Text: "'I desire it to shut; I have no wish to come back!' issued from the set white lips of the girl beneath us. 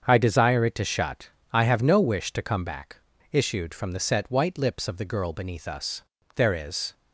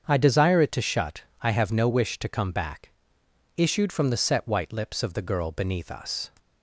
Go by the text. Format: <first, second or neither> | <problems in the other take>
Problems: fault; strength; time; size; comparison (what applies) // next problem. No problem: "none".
second | starts louder than the rest; until 1.0 s; 7 dB; also in the second // goes on to say "There is"; from 6.3 s on; 0.58 s long